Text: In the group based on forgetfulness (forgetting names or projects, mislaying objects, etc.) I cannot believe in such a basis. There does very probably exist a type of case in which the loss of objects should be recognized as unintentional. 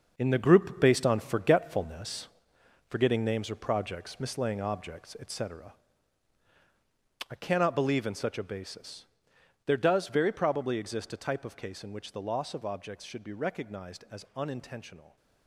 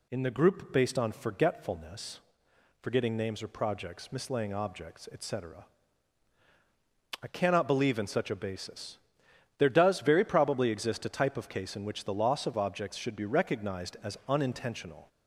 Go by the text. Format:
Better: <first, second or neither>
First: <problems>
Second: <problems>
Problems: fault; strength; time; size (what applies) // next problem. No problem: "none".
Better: second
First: gets quieter; strong; throughout; 9 dB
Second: none